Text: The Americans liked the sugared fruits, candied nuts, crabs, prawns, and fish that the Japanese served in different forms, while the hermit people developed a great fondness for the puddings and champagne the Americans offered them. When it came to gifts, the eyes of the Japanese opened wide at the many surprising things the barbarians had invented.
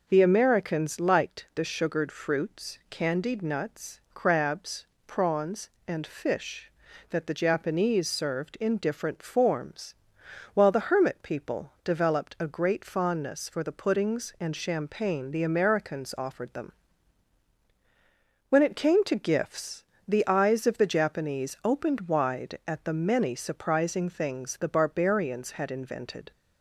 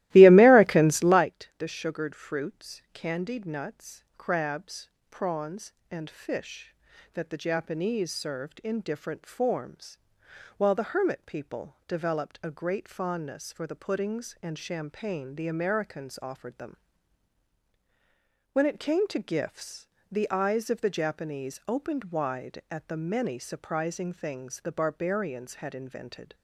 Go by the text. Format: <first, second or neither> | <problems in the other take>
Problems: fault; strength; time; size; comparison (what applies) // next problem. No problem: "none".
first | starts louder than the rest; strong; until 1.3 s; 17 dB